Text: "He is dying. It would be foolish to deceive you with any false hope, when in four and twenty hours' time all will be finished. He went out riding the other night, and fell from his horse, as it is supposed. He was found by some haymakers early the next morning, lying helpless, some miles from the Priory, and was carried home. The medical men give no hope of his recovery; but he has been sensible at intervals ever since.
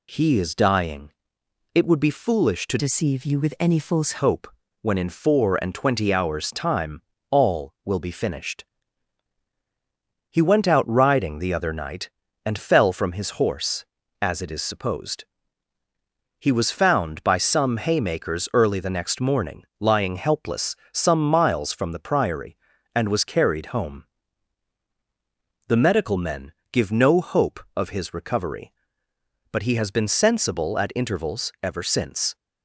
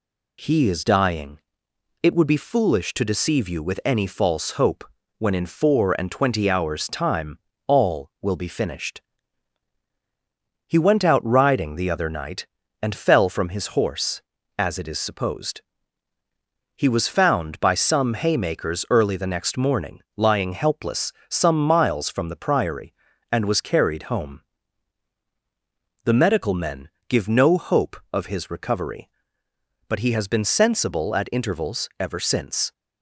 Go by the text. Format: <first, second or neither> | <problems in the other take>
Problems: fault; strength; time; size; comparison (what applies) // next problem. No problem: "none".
second | changes voice from "deceive" to "false"; from 2.7 to 4.1 s; 1.4 s long // pauses between "time" and "all"; slight; at 7.0 s; 0.28 s long; slight in the second // pauses between "men" and "give"; slight; at 26.5 s; 0.18 s long; slight in the second